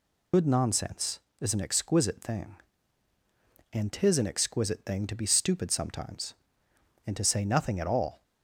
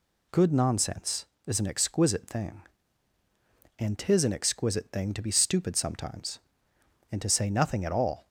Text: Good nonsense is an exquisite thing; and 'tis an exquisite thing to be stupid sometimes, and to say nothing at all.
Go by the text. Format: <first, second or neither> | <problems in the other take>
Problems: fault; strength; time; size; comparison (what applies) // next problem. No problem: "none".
second | loses the start of "Good"; at 0.3 s; 90 ms